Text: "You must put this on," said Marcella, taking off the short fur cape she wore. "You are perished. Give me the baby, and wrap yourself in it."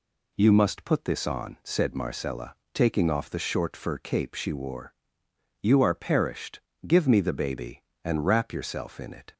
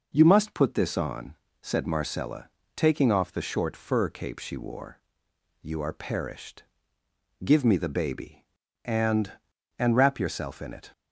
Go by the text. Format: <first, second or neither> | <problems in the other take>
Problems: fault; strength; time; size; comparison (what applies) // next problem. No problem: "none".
first | says "and" twice; at 9.7 s